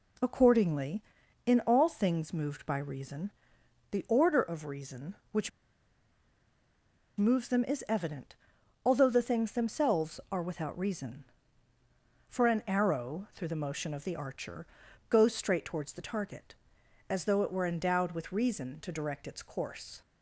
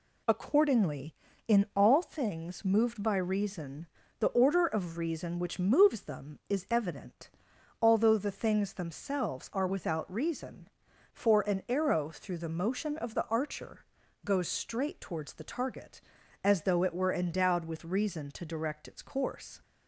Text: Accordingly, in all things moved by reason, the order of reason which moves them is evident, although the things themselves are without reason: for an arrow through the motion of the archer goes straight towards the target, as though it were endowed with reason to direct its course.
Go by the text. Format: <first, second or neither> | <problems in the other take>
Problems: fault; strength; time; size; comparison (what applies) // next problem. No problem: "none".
second | pauses between "which" and "moves"; strong; at 5.5 s; 1.6 s long // pauses between "archer" and "goes"; noticeable; at 14.6 s; 0.46 s long; also in the second